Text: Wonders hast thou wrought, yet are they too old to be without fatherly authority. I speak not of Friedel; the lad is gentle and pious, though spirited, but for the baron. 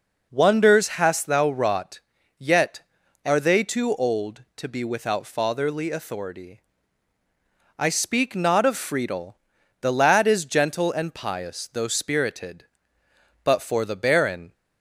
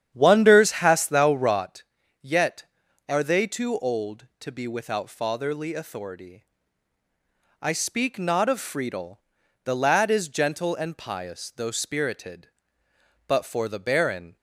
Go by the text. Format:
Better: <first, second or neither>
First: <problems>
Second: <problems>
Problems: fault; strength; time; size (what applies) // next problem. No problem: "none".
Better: first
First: none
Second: starts louder than the rest; strong; until 1.6 s; 9 dB